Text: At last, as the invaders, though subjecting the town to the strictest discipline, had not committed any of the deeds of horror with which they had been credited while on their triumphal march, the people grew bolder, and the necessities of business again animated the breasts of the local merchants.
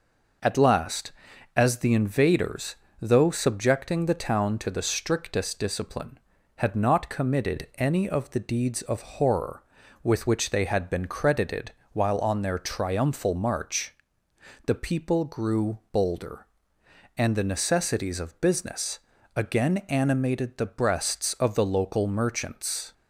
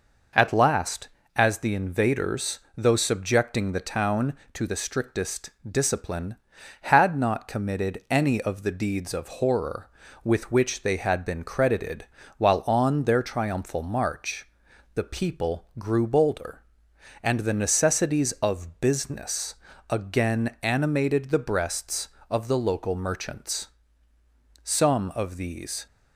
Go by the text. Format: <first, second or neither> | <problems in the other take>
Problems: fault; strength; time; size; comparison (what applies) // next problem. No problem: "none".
first | pauses between "strictest" and "discipline"; slight; at 5.4 s; 0.18 s long // pauses between "credited" and "while"; slight; at 12.0 s; 0.32 s long; slight in the first // pauses between "business" and "again"; slight; at 19.5 s; 0.34 s long; slight in the first // goes on to say "Some of these"; noticeable; from 24.6 s on; 1.2 s long